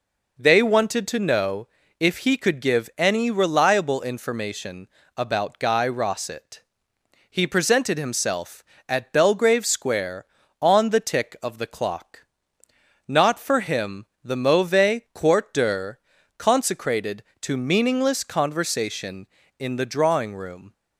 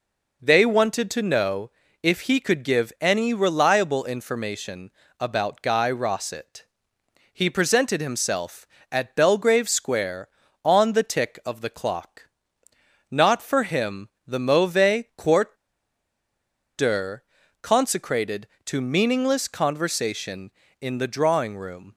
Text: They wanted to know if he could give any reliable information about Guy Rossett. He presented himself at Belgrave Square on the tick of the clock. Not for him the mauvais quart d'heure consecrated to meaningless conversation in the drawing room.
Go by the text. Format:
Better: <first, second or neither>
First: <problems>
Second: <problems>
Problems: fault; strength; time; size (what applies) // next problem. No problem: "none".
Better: first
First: pauses between "know" and "if"; slight; at 1.6 s; 0.32 s long // pauses between "information" and "about"; slight; at 4.8 s; 0.28 s long // pauses between "him" and "the"; slight; at 14.0 s; 0.18 s long // pauses between "d'heure" and "consecrated"; at 15.9 s; 0.40 s long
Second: pauses between "know" and "if"; slight; at 1.7 s; 0.32 s long // pauses between "information" and "about"; slight; at 4.9 s; 0.28 s long // pauses between "him" and "the"; slight; at 14.0 s; 0.18 s long // pauses between "quart" and "d'heure"; at 15.5 s; 1.2 s long // pauses between "d'heure" and "consecrated"; at 17.2 s; 0.40 s long